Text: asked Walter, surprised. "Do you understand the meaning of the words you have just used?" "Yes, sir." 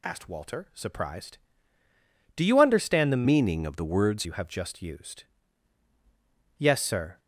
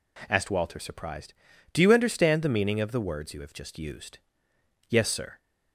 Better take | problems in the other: second | changes voice from "meaning" to "words"; from 3.2 to 4.2 s; 1.0 s long

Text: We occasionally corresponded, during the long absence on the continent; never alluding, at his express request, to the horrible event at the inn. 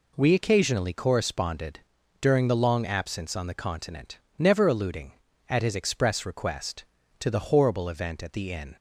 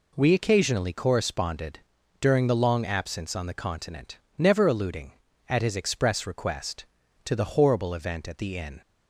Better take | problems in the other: neither | none

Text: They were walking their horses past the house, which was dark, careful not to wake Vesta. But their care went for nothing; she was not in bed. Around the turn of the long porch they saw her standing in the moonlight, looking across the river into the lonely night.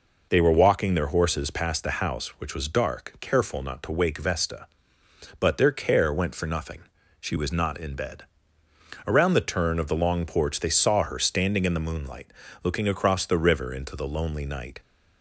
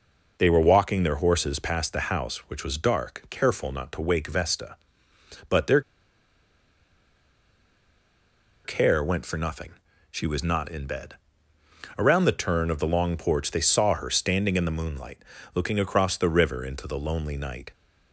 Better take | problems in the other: first | pauses between "their" and "care"; strong; at 5.8 s; 2.8 s long

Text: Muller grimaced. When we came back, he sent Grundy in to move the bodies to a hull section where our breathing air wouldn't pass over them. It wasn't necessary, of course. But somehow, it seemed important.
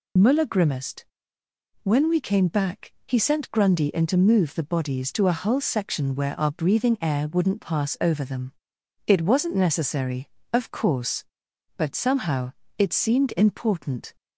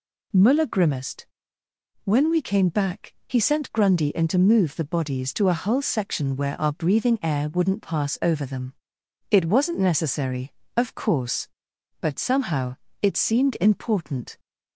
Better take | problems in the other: second | loses the start of "Muller"; at 0.1 s; 35 ms

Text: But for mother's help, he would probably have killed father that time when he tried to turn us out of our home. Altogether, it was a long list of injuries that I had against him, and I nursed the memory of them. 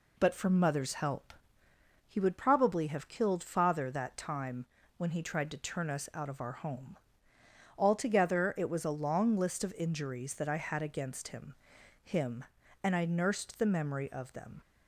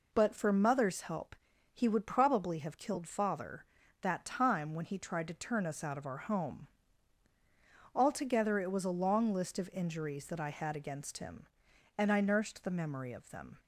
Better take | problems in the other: second | pauses between "time" and "when"; slight; at 4.6 s; 0.32 s long // says "him" twice; at 12.0 s

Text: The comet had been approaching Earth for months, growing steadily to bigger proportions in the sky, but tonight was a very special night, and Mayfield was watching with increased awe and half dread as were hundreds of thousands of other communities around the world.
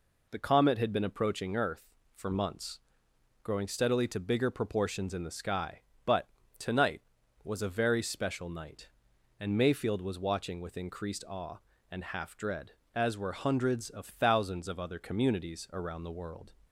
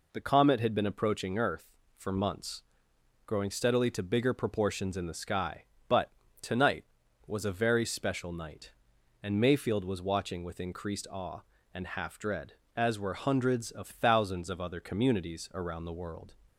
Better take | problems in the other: neither | pauses between "but" and "tonight"; slight; the same in both

